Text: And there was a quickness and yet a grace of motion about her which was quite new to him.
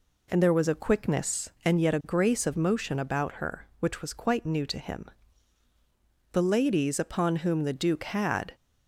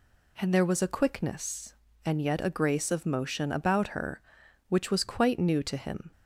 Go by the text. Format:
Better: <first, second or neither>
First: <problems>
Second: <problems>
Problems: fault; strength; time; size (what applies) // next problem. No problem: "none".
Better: second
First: goes on to say "The ladies upon whom the Duke had"; strong; from 6.3 s on; 2.2 s long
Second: none